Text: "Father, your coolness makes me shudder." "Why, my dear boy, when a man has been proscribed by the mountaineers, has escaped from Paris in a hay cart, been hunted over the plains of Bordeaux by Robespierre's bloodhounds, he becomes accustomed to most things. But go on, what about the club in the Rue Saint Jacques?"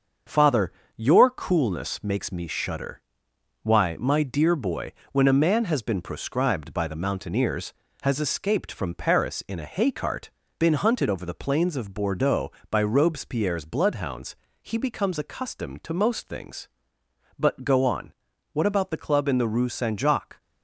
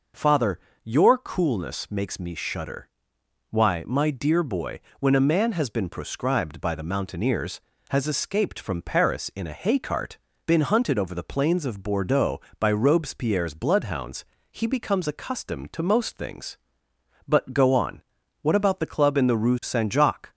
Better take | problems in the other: second | gets quieter; noticeable; throughout; 5 dB

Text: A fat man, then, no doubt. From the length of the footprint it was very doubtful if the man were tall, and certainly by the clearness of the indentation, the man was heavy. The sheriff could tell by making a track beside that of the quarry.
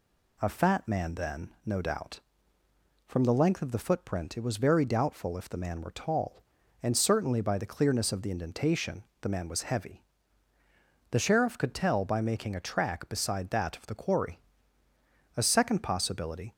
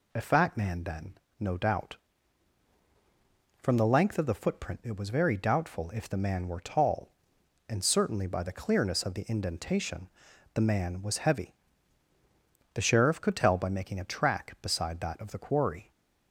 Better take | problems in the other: second | goes on to say "A second possibility"; noticeable; from 15.3 s on; 1.1 s long

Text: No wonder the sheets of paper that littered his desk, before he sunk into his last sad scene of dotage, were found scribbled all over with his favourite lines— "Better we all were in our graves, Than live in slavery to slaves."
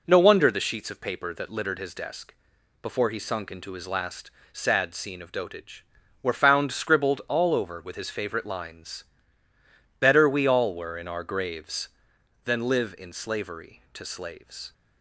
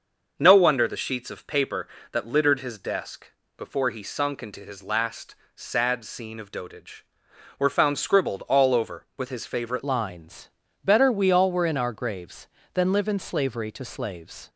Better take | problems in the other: first | starts louder than the rest; until 1.3 s; 6.5 dB // pauses between "last" and "sad"; slight; at 5.3 s; 0.22 s long; slight in the first // changes voice at "lines"; from 9.8 s on; 4.6 s long

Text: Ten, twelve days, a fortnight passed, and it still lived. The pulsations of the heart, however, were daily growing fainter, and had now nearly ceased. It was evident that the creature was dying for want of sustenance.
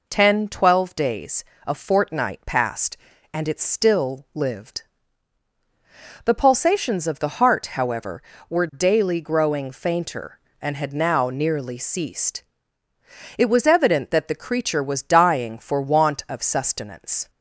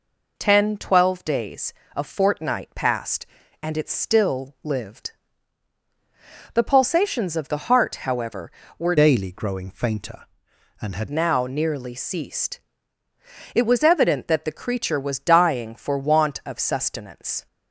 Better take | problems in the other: first | changes voice from "daily" to "had"; from 8.9 to 11.0 s; 2.1 s long

